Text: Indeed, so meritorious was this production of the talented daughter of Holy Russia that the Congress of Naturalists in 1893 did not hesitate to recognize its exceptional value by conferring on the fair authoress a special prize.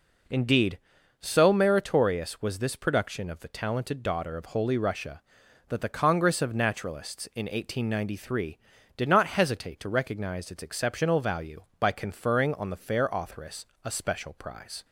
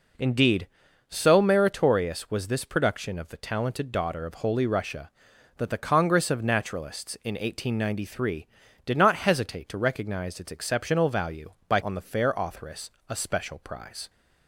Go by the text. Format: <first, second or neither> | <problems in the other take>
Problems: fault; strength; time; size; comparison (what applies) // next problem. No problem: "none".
first | skips "conferring"; at 11.8 s // pauses between "authoress" and "a"; slight; at 12.8 s; 0.18 s long; slight in the first